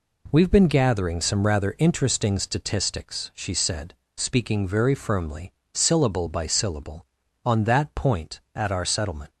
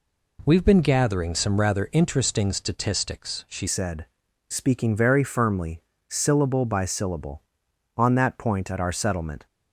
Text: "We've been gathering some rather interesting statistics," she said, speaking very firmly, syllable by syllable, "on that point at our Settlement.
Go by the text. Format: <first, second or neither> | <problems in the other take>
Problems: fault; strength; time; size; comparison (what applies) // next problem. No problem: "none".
first | changes voice at "said"; from 3.6 s on; 5.8 s long